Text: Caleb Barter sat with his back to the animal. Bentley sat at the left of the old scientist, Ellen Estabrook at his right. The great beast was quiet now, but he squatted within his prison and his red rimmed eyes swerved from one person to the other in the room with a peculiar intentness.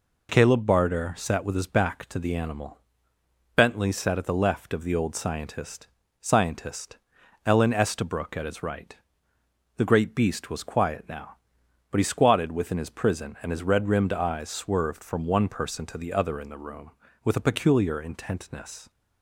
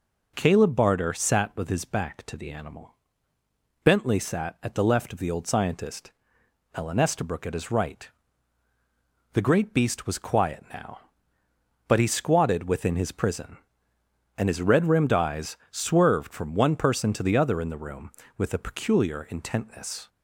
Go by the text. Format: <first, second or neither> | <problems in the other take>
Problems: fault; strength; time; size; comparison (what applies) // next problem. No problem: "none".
second | says "scientist" twice; at 6.2 s